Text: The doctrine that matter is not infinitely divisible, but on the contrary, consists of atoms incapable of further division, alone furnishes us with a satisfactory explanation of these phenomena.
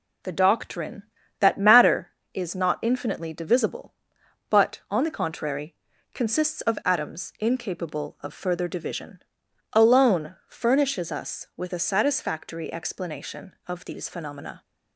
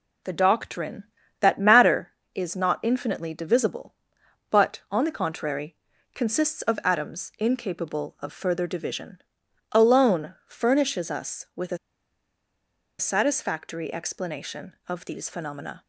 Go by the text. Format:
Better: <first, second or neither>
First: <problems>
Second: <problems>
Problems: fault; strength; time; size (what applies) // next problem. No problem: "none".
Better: first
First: none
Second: pauses between "a" and "satisfactory"; at 11.7 s; 1.2 s long